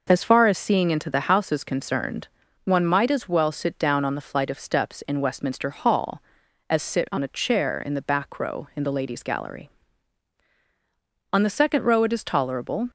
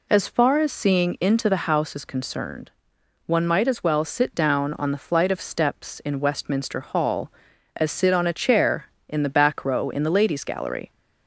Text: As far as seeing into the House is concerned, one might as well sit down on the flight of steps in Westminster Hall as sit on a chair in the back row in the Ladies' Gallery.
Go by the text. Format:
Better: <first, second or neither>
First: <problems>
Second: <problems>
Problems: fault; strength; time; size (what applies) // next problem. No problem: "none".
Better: second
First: goes on to say "On the second row it is tolerable"; from 11.3 s on; 1.5 s long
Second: none